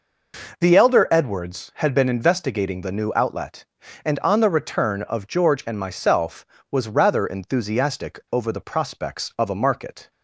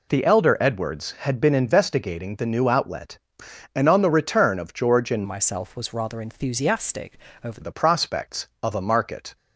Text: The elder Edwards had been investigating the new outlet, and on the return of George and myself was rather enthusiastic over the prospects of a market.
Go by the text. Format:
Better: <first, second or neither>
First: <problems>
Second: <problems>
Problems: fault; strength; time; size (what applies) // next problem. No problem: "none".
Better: first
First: none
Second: changes voice from "myself" to "over"; from 5.2 to 7.6 s; 2.4 s long // pauses between "enthusiastic" and "over"; slight; at 7.1 s; 0.32 s long